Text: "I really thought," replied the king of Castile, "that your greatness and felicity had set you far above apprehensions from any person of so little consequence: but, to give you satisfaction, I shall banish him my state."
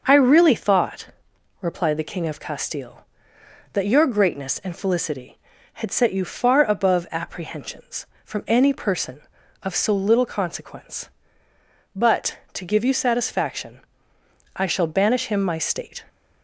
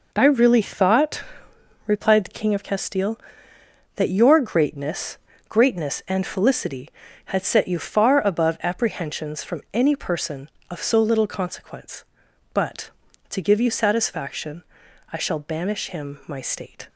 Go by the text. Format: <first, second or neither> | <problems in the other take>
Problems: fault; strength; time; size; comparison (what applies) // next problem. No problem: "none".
first | says "greatness" twice; at 5.4 s